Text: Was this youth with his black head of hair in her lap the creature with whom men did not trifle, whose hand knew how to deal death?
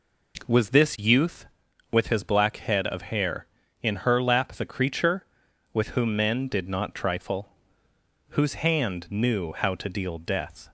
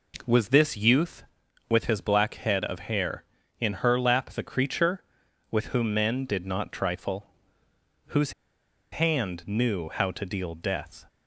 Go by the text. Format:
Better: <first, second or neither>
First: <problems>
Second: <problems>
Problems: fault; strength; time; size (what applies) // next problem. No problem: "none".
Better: first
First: none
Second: pauses between "whose" and "hand"; noticeable; at 8.3 s; 0.61 s long